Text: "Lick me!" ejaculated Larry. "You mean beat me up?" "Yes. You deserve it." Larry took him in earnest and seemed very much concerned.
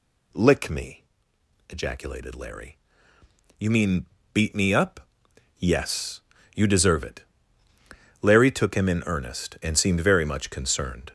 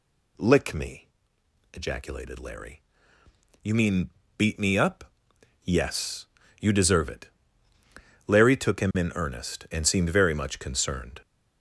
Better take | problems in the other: neither | pauses between "mean" and "beat"; slight; the same in both

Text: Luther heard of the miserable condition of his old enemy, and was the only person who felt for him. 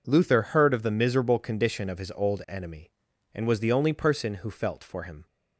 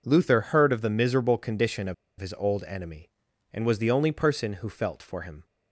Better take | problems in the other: first | pauses between "of" and "his"; slight; at 1.9 s; 0.24 s long

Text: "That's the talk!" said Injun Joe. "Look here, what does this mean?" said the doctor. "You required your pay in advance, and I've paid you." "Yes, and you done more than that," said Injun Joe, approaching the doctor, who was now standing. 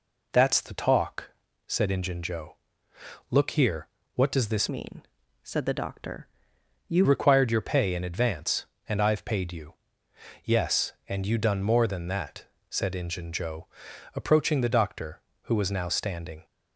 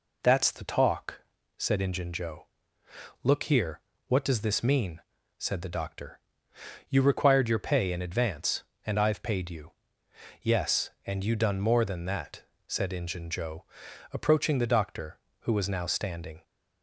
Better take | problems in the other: second | changes voice from "mean" to "You"; from 4.6 to 7.0 s; 2.4 s long

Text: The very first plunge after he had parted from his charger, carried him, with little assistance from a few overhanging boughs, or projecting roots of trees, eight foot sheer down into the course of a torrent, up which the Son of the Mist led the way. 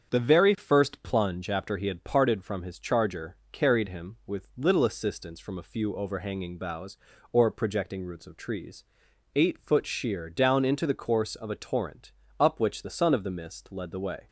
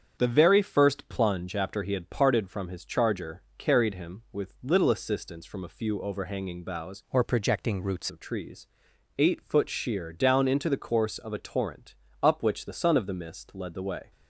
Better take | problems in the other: first | starts louder than the rest; strong; until 1.2 s; 7.5 dB; strong in the first // changes voice from "or" to "roots"; from 7.0 to 8.1 s; 1.1 s long

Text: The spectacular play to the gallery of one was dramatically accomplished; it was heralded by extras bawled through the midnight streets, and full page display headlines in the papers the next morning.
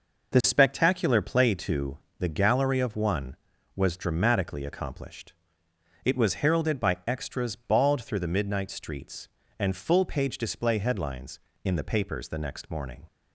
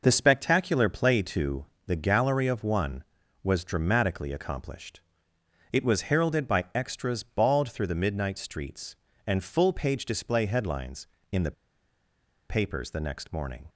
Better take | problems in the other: first | pauses between "to" and "the"; slight; at 1.6 s; 0.22 s long; slight in the first // pauses between "the" and "papers"; noticeable; at 11.5 s; 0.96 s long

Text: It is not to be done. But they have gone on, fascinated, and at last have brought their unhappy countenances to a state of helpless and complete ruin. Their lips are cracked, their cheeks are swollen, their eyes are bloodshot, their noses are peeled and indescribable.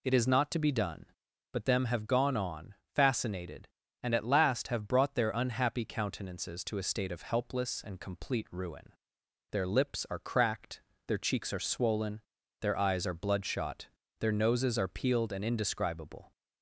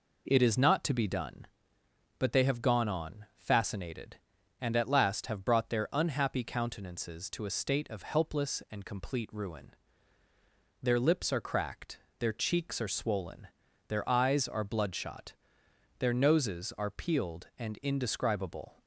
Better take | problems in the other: second | says "them" for "they"; at 1.6 s

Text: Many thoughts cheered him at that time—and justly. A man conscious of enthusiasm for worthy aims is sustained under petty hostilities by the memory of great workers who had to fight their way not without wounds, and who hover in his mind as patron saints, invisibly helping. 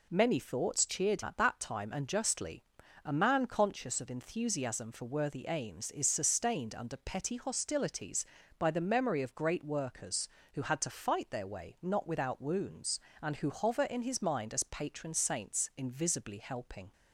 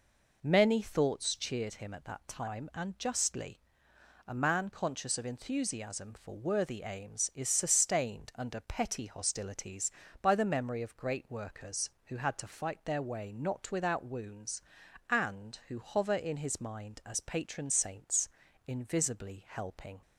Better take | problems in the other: second | skips "him"; at 1.2 s

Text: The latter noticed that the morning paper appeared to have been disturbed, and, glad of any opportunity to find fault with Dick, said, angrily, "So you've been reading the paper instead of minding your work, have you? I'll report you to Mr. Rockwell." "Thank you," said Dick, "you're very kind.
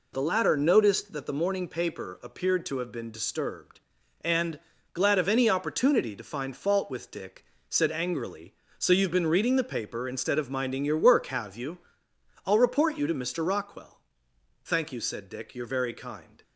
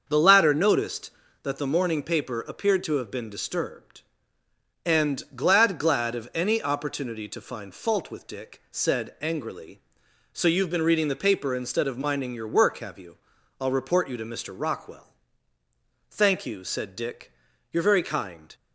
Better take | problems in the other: first | starts louder than the rest; until 1.0 s; 6.5 dB // says "glad" twice; at 5.7 s

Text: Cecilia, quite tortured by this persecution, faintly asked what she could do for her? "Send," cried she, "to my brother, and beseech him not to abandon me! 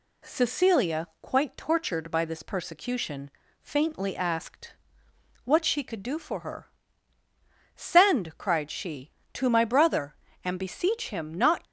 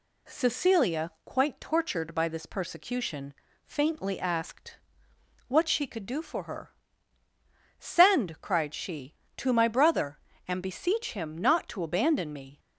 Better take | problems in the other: second | pauses between "asked" and "what"; noticeable; at 4.7 s; 0.72 s long; noticeable in the second // stops before "to abandon me"; at 11.6 s

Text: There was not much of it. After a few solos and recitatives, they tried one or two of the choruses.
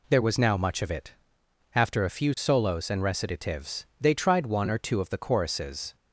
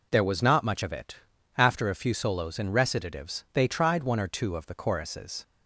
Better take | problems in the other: second | says "now" for "not"; at 0.3 s

